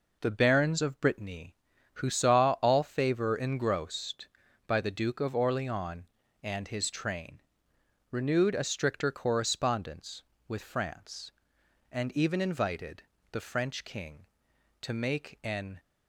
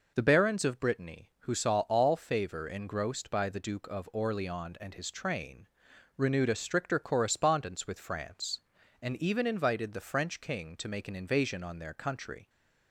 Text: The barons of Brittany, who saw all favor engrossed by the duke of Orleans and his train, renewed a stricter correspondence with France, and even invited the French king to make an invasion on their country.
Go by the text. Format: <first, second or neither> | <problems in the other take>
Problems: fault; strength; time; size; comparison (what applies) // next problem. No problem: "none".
second | pauses between "invited" and "the"; slight; at 13.0 s; 0.28 s long // stops before "invasion on their country"; at 15.7 s